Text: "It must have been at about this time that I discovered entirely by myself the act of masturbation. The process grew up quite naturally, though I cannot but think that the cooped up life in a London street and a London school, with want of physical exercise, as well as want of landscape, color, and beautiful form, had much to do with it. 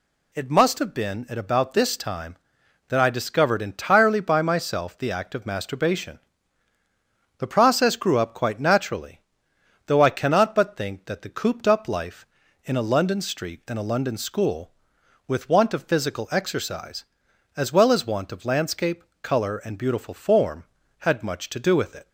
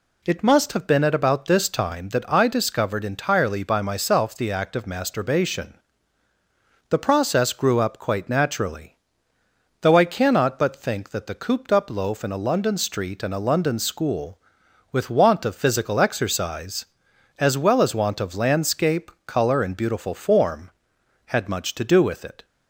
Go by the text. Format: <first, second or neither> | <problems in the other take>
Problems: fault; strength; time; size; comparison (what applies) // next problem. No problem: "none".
first | says "loaf" for "life"; at 11.9 s